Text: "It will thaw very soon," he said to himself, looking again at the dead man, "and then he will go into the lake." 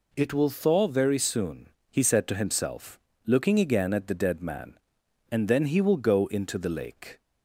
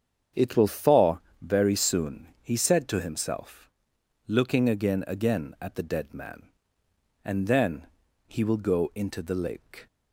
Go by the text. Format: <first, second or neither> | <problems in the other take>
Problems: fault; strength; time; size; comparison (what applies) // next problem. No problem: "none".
first | starts louder than the rest; strong; until 1.5 s; 8 dB // pauses between "thaw" and "very"; slight; at 1.1 s; 0.22 s long // says "again" twice; at 5.0 s // pauses between "then" and "he"; at 7.8 s; 0.40 s long